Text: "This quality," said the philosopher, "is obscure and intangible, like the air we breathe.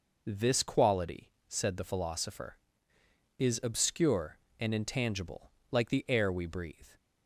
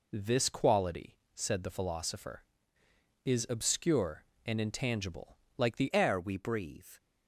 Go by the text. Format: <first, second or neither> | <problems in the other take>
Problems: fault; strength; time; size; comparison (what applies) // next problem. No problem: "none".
first | changes voice at "air"; from 5.9 s on; 1.0 s long